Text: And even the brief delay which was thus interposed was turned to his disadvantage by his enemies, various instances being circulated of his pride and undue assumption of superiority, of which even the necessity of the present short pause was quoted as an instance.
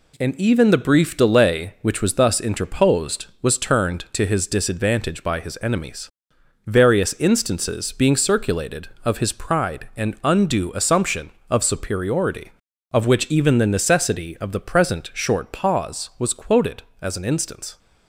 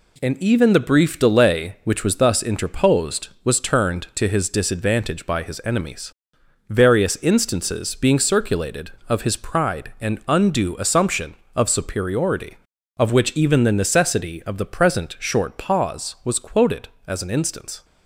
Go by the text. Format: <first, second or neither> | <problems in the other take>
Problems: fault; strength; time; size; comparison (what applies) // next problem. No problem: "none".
neither | none